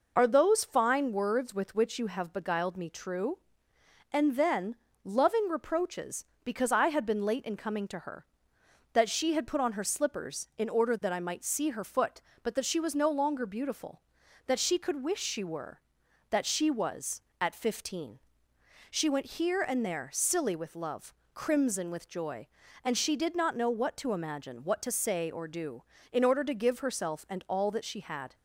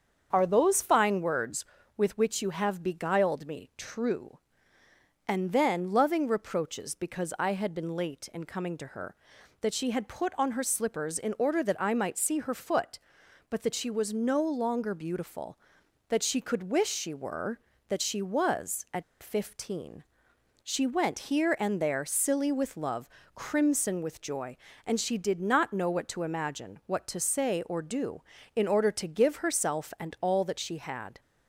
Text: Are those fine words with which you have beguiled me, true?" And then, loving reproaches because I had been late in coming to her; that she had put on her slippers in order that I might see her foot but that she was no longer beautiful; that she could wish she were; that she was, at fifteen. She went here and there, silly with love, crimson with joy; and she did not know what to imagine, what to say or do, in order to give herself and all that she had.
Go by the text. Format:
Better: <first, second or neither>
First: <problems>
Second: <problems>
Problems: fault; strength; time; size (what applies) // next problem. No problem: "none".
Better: first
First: none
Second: starts louder than the rest; strong; until 1.3 s; 7 dB // pauses between "at" and "fifteen"; slight; at 19.0 s; 0.18 s long